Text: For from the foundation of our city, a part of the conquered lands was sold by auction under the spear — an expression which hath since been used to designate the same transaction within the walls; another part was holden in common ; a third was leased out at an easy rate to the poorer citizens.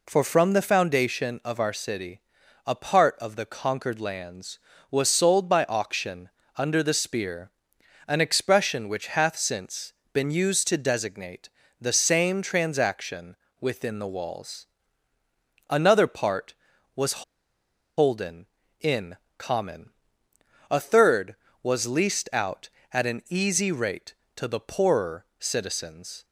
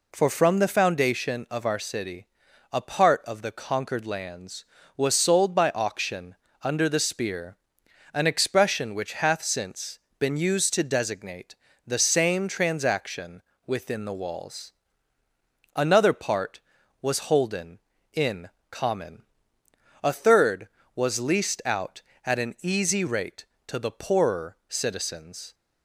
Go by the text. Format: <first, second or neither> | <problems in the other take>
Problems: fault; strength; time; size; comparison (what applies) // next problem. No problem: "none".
second | pauses between "auction" and "under"; slight; at 6.2 s; 0.28 s long; slight in the second // pauses between "since" and "been"; slight; at 9.9 s; 0.20 s long; slight in the second // pauses between "designate" and "the"; slight; at 11.4 s; 0.32 s long; slight in the second // pauses between "transaction" and "within"; slight; at 13.3 s; 0.26 s long; slight in the second // pauses between "was" and "holden"; noticeable; at 17.2 s; 0.74 s long // pauses between "in" and "common"; slight; at 19.1 s; 0.20 s long; slight in the second // pauses between "poorer" and "citizens"; slight; at 25.2 s; 0.16 s long